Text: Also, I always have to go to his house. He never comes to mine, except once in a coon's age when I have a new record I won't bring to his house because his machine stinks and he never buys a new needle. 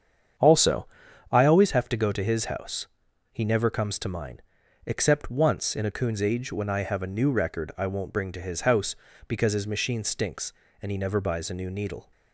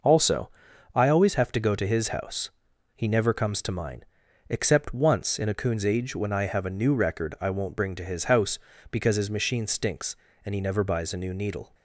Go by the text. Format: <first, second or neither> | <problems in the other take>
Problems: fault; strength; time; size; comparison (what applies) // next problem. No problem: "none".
second | starts louder than the rest; strong; until 1.8 s; 8 dB